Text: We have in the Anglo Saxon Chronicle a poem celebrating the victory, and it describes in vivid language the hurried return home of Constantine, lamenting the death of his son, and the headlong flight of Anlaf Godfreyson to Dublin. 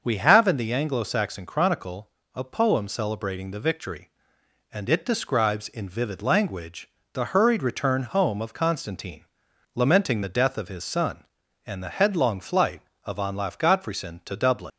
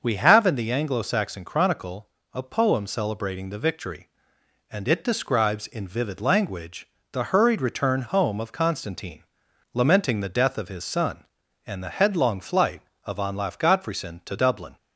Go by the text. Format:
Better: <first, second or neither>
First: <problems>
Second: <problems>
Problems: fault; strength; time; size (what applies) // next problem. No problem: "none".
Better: second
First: starts louder than the rest; until 1.0 s; 6.5 dB // pauses between "Chronicle" and "a"; slight; at 2.0 s; 0.24 s long // pauses between "language" and "the"; slight; at 6.8 s; 0.24 s long // leaves "Dublin" unfinished; at 14.7 s; 80 ms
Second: starts louder than the rest; until 1.0 s; 6.5 dB // pauses between "Chronicle" and "a"; slight; at 2.0 s; 0.24 s long // pauses between "language" and "the"; slight; at 6.8 s; 0.24 s long